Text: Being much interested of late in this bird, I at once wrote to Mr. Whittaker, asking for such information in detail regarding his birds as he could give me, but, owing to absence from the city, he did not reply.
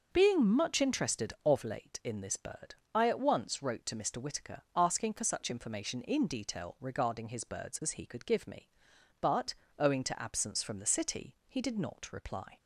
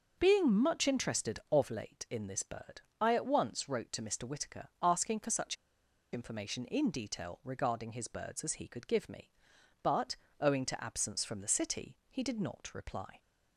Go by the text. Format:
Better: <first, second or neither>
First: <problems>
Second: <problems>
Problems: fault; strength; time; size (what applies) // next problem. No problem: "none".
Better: first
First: none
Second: pauses between "such" and "information"; noticeable; at 5.5 s; 0.58 s long